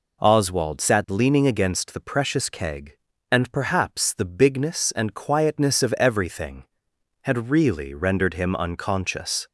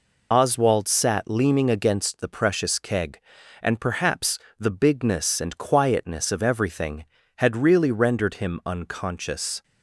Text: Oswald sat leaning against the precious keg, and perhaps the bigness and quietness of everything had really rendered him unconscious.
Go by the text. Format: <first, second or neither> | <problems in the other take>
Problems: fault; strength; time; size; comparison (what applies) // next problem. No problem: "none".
first | loses the start of "Oswald"; at 0.3 s; 25 ms // pauses between "perhaps" and "the"; slight; at 4.3 s; 0.22 s long